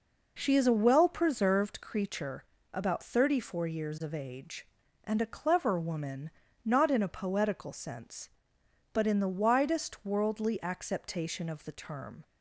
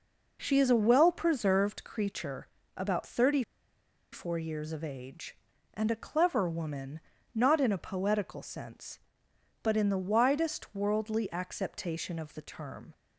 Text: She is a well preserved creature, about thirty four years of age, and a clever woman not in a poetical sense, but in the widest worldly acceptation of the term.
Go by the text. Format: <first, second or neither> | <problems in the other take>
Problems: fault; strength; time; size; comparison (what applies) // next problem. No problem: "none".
first | pauses between "thirty" and "four"; noticeable; at 3.4 s; 0.70 s long // pauses between "woman" and "not"; slight; at 7.0 s; 0.32 s long; slight in the first